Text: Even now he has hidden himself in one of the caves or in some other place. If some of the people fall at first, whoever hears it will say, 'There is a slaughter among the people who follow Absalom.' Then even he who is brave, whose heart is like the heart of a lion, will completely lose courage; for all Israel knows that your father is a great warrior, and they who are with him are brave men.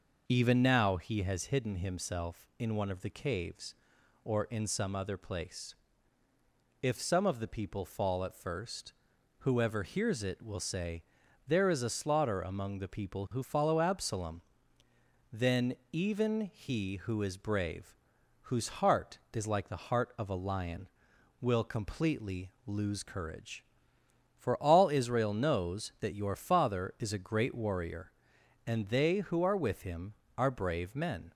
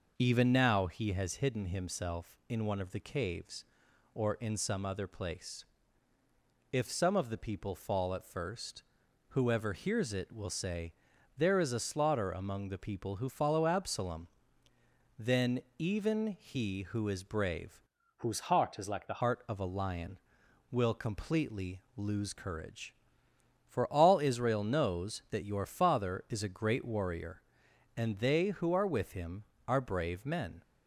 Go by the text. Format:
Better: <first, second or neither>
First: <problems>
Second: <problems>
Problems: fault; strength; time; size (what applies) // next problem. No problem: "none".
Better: first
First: pauses between "Then" and "even"; slight; at 15.7 s; 0.16 s long // pauses between "completely" and "lose"; slight; at 22.5 s; 0.16 s long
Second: pauses between "Then" and "even"; slight; at 15.6 s; 0.16 s long // changes voice from "whose" to "the"; from 18.1 to 19.2 s; 1.1 s long // pauses between "completely" and "lose"; slight; at 21.8 s; 0.16 s long